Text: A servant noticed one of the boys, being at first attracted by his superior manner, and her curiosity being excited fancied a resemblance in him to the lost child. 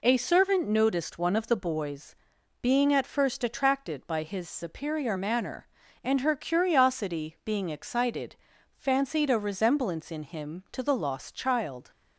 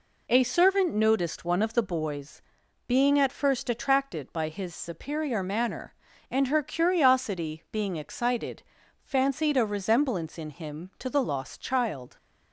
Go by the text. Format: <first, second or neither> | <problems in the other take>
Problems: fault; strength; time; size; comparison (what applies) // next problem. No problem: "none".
neither | pauses between "excited" and "fancied"; the same in both